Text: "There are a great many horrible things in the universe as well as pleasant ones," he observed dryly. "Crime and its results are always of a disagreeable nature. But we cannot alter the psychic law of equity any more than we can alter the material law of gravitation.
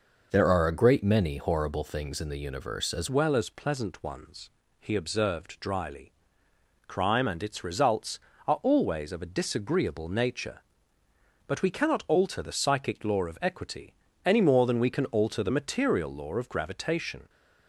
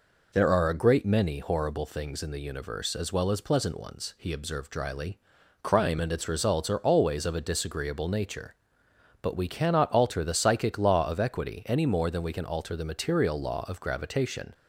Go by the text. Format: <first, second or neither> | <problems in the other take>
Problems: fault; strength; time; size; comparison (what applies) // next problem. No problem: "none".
second | changes voice at "well"; from 3.0 s on; 14.2 s long // pauses between "equity" and "any"; slight; at 13.9 s; 0.32 s long